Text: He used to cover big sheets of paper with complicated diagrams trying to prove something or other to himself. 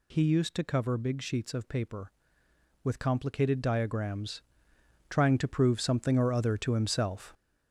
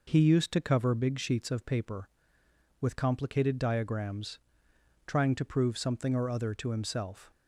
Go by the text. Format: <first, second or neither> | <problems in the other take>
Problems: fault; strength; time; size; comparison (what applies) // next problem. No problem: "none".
second | gets louder; throughout; 6.5 dB // pauses between "diagrams" and "trying"; noticeable; at 4.4 s; 0.68 s long; noticeable in the second